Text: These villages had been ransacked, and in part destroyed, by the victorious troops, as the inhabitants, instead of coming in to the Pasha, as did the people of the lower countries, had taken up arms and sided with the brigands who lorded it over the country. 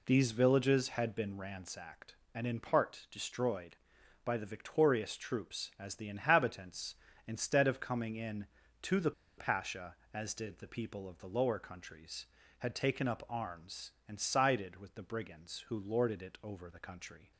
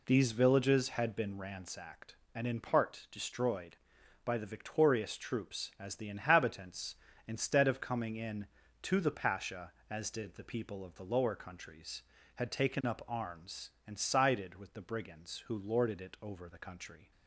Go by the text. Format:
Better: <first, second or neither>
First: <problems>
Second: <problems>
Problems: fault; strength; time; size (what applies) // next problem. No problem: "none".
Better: second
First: pauses between "the" and "Pasha"; slight; at 9.1 s; 0.26 s long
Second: none